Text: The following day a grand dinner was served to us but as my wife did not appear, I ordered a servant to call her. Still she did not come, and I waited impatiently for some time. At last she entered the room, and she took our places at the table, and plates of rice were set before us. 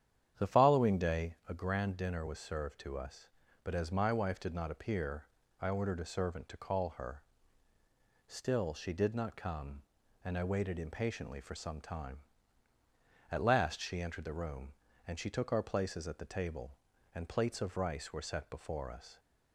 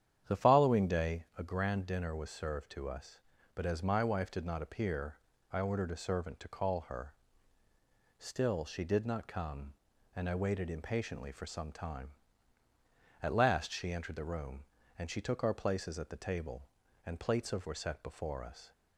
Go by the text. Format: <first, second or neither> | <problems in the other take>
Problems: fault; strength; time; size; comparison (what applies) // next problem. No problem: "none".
first | starts louder than the rest; strong; until 1.3 s; 9.5 dB; strong in the first // skips "rice"; at 17.6 s